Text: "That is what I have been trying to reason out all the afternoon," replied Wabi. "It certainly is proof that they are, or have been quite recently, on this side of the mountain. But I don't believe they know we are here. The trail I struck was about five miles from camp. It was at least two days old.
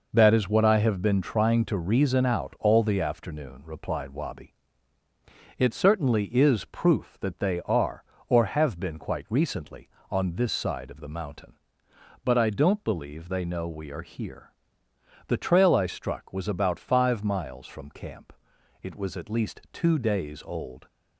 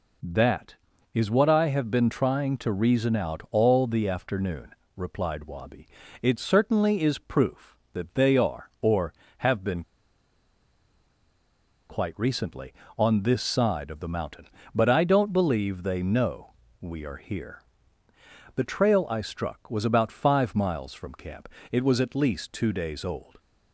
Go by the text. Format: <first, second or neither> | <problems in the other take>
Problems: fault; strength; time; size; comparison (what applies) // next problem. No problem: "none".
first | pauses between "been" and "quite"; strong; at 9.8 s; 2.0 s long // pauses between "know" and "we"; slight; at 16.5 s; 0.26 s long